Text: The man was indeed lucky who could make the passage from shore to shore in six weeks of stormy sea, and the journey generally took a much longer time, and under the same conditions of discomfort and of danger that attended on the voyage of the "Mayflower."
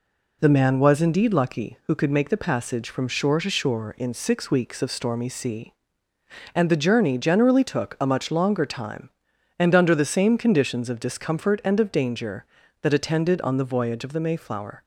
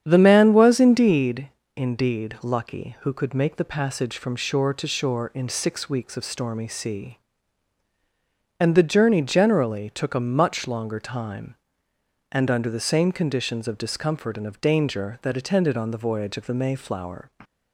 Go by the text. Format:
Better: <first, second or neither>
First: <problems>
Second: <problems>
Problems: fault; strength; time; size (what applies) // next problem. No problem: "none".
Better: first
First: none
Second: starts louder than the rest; strong; until 1.0 s; 8.5 dB // says "indeed" twice; at 1.7 s